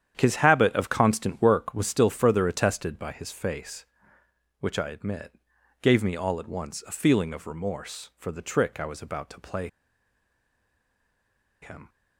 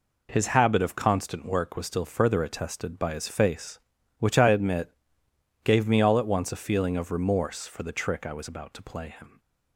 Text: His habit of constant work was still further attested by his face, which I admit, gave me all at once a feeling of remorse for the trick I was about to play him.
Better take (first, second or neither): second